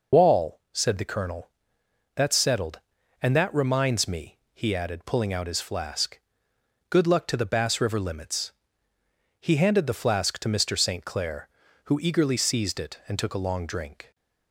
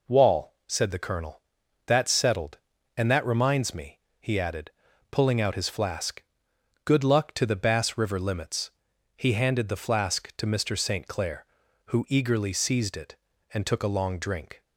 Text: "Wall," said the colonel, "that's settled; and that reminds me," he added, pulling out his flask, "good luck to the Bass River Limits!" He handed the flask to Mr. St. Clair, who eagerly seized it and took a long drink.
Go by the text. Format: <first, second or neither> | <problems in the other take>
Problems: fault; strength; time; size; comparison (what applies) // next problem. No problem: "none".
second | loses the start of "Wall"; at 0.1 s; 85 ms